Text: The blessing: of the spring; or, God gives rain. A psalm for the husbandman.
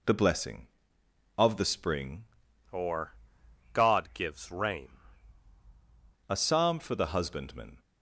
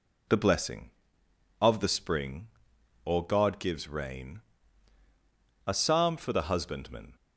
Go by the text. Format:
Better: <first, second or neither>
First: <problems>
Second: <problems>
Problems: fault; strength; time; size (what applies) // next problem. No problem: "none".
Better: second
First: changes voice from "or" to "rain"; from 2.7 to 4.9 s; 2.2 s long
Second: none